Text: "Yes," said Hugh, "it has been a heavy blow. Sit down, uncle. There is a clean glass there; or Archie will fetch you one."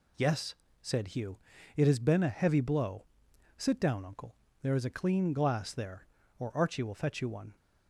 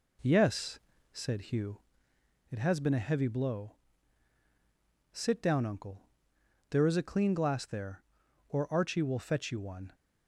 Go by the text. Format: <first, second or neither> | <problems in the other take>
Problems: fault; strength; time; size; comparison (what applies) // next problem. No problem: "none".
first | starts louder than the rest; until 2.0 s; 4 dB